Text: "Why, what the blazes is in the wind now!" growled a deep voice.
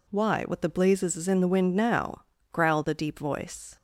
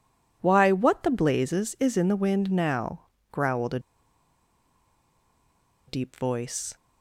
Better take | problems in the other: first | pauses between "a" and "deep"; strong; at 3.7 s; 2.0 s long

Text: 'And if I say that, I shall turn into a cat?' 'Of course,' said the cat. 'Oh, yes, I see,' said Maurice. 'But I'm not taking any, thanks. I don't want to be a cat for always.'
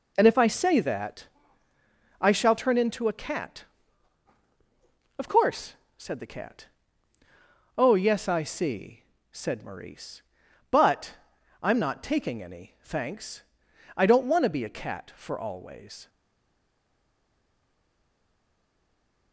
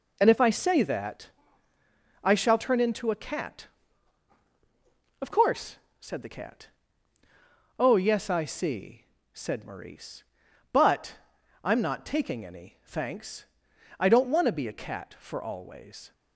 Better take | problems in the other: second | pauses between "But" and "I'm"; noticeable; at 11.1 s; 0.46 s long; noticeable in the second // stays silent after the last word; strong; from 16.0 s on; 3.3 s long

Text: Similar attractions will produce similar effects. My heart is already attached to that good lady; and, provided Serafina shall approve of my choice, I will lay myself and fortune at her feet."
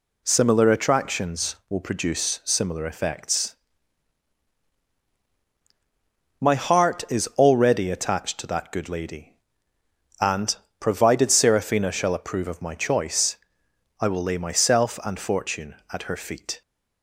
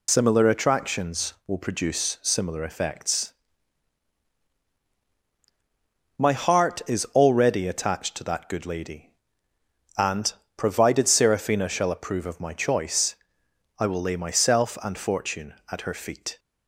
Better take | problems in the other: first | loses the start of "Similar"; at 0.0 s; 55 ms

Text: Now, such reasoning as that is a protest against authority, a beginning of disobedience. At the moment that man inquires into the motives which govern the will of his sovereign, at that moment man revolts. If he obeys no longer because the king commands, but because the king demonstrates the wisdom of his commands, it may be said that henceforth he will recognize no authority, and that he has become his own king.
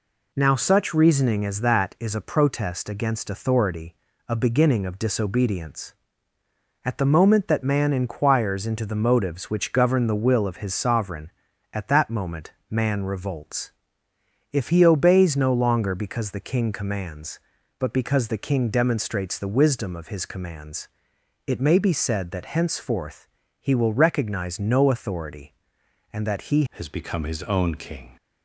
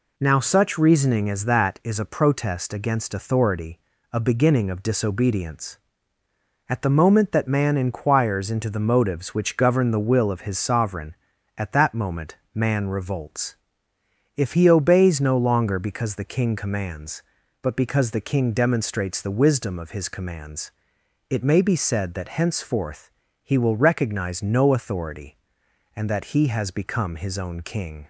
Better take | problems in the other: second | pauses between "moment" and "man"; slight; at 12.5 s; 0.18 s long; slight in the second // pauses between "henceforth" and "he"; slight; at 23.2 s; 0.34 s long; slight in the second // changes voice at "has"; from 26.7 s on; 1.4 s long

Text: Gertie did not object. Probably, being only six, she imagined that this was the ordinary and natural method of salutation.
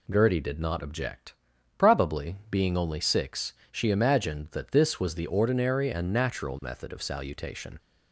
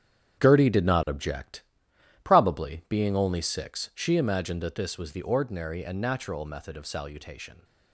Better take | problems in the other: first | gets quieter; strong; throughout; 10.5 dB

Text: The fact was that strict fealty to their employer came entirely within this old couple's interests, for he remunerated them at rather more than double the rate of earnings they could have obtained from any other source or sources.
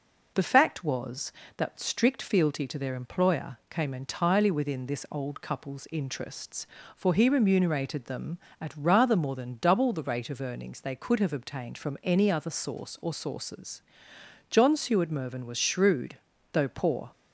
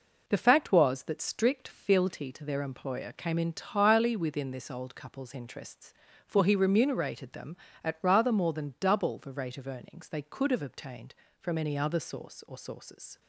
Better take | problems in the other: second | goes on to say "John Seward Mervyn was shrewd though poor"; strong; from 14.4 s on; 2.6 s long

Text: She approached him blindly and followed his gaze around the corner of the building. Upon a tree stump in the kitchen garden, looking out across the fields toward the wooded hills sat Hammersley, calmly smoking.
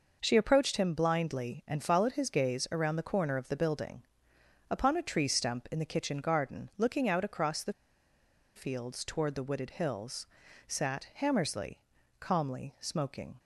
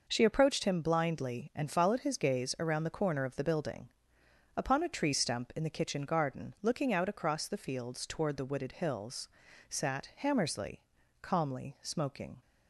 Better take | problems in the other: second | pauses between "the" and "fields"; noticeable; at 7.7 s; 0.83 s long // pauses between "hills" and "sat"; at 10.2 s; 0.42 s long; also in the second

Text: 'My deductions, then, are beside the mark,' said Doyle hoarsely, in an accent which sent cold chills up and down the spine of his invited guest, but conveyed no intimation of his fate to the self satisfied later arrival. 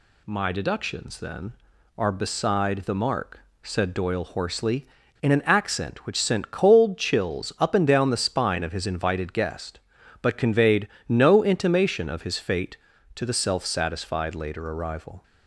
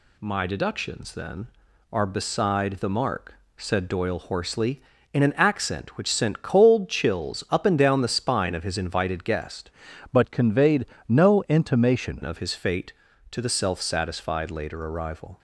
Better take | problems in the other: first | changes voice from "but" to "intimation"; from 10.1 to 12.2 s; 2.1 s long // pauses between "conveyed" and "no"; slight; at 10.8 s; 0.24 s long; slight in the first

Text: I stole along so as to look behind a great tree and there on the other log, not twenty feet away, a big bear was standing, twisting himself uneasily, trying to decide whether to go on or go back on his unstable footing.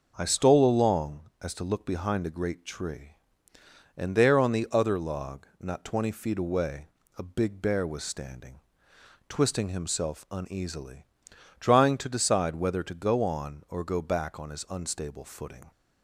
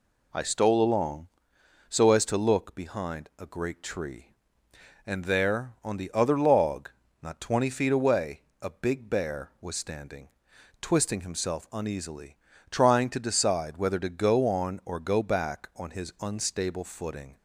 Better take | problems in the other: second | skips "so"; at 1.3 s

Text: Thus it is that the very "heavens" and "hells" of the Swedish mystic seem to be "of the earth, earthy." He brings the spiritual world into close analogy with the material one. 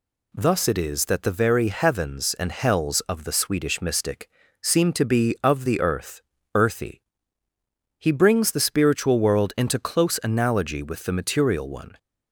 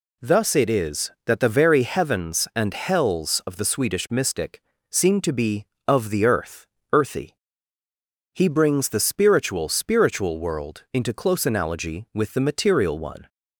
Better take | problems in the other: first | pauses between "mystic" and "seem"; slight; at 4.6 s; 0.30 s long; slight in the first // says "spiritual" twice; at 9.6 s

